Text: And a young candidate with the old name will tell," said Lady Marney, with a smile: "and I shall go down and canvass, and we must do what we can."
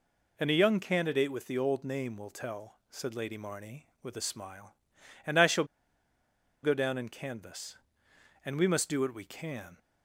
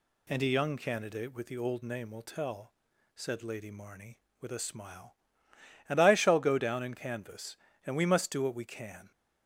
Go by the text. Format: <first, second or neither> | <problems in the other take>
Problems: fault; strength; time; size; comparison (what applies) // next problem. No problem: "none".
second | pauses between "shall" and "go"; at 5.6 s; 0.98 s long